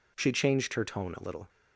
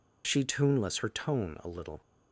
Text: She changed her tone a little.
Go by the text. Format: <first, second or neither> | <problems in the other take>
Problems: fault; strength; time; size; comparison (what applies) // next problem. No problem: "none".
first | says "tuneless" for "changed"; at 0.4 s